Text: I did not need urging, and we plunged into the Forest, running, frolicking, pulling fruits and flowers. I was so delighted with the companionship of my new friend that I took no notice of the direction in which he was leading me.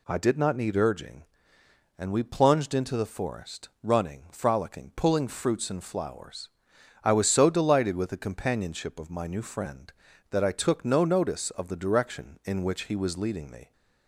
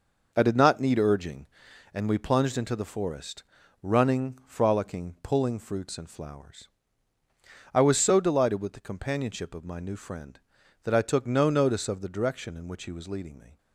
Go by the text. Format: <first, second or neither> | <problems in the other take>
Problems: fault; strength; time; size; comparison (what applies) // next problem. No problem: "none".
first | gets quieter; strong; throughout; 7.5 dB